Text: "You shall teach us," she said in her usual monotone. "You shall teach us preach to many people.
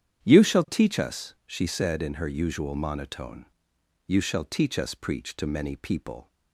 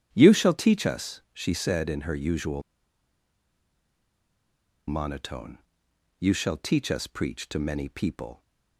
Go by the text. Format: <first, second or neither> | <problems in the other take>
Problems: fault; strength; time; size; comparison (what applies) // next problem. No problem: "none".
first | starts louder than the rest; strong; until 1.1 s; 9 dB; strong in the first // pauses between "usual" and "monotone"; strong; at 2.6 s; 2.2 s long